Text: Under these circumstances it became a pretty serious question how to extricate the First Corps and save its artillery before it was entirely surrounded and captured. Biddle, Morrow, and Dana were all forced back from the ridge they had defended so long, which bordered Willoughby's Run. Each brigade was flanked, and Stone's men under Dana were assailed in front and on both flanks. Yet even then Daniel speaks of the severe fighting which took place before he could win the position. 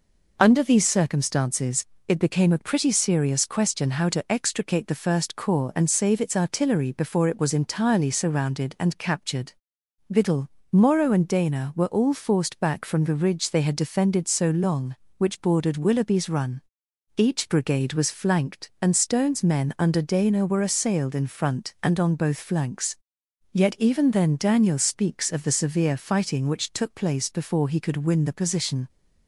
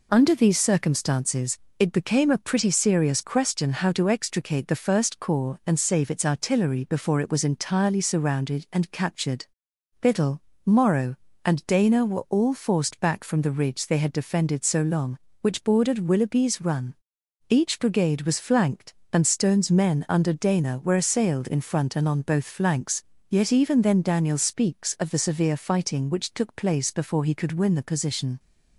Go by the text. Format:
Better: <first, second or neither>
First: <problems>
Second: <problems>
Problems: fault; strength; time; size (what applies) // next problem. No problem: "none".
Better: neither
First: pauses between "circumstances" and "it"; slight; at 1.8 s; 0.20 s long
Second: pauses between "circumstances" and "it"; slight; at 1.5 s; 0.18 s long